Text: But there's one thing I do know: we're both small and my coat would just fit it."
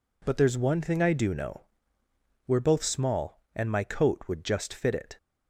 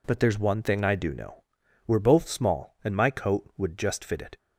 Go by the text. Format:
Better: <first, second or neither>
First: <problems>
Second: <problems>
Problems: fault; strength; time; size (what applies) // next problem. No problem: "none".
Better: neither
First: none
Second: none